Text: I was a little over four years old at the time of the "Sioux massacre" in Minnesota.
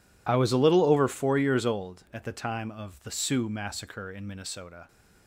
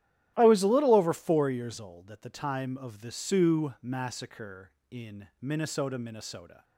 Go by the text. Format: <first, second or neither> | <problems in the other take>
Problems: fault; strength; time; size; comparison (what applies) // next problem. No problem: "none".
first | starts louder than the rest; strong; until 1.3 s; 12 dB // says "Minnesota" twice; at 5.9 s